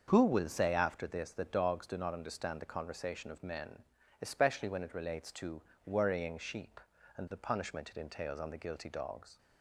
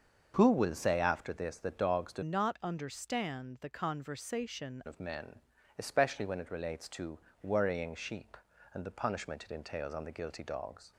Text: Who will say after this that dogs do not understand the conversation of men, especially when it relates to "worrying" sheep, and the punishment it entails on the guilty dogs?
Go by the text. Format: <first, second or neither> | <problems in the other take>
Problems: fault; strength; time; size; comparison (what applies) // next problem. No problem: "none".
first | starts louder than the rest; until 1.3 s; 6.5 dB; also in the first // changes voice from "not" to "conversation"; from 2.2 to 4.8 s; 2.6 s long // pauses between "to" and "worrying"; slight; at 7.1 s; 0.24 s long; slight in the first